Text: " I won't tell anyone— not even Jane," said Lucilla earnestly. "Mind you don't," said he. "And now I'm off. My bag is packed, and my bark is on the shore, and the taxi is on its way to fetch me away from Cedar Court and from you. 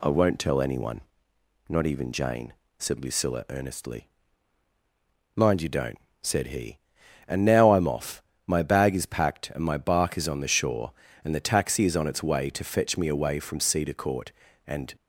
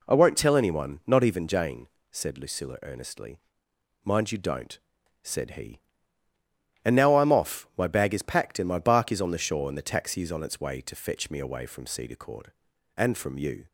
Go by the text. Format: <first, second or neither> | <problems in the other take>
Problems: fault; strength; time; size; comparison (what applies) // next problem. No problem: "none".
second | stops before "from you"; at 14.9 s